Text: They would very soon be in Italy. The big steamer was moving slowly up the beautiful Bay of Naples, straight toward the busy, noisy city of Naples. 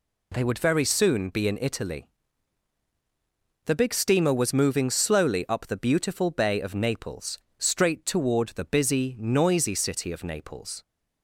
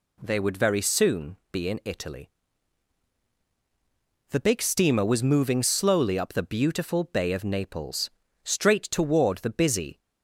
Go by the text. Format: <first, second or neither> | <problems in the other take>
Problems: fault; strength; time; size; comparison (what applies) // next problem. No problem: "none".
first | stops before "noisy city of Naples"; at 9.9 s